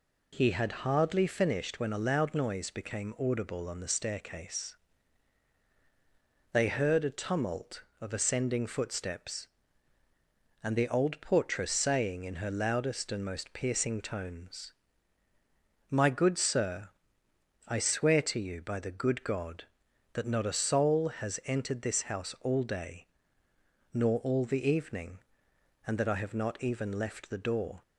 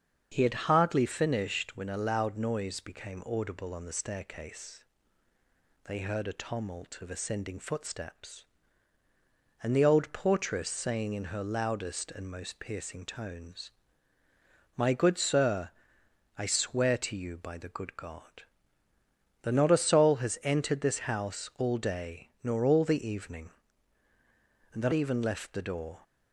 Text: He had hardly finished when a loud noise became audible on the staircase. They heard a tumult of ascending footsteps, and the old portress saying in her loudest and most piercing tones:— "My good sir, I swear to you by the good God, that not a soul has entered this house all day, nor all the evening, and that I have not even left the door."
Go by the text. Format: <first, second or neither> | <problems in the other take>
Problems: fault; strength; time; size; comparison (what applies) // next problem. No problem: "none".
first | starts louder than the rest; until 1.3 s; 7 dB // skips "I have not"; at 24.9 s